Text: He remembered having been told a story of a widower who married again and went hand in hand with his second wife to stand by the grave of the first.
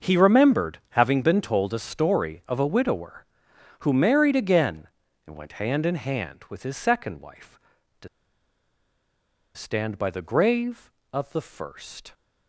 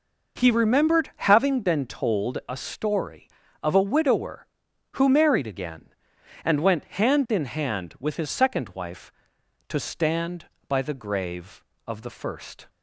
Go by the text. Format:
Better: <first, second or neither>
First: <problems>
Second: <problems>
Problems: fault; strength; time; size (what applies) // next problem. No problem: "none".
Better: second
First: starts louder than the rest; until 1.1 s; 6 dB // pauses between "to" and "stand"; strong; at 8.0 s; 1.4 s long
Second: none